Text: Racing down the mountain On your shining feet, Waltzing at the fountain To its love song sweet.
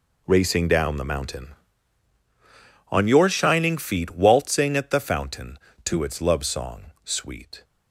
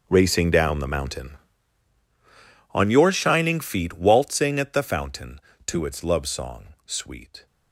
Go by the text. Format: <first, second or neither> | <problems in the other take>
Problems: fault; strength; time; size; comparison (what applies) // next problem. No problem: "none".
first | gets quieter; strong; throughout; 17 dB